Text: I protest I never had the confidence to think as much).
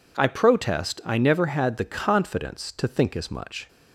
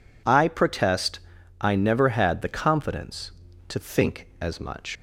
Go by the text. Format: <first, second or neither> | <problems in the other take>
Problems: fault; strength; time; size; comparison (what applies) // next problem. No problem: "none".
first | pauses between "protest" and "I"; at 1.1 s; 0.42 s long // leaves "much" unfinished; at 4.9 s; 100 ms